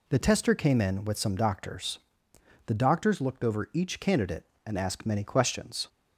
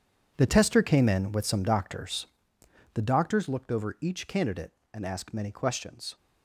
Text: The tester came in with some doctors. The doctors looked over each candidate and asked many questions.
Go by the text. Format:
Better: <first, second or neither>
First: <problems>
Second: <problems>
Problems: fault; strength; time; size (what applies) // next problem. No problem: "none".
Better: first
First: none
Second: gets quieter; strong; throughout; 13 dB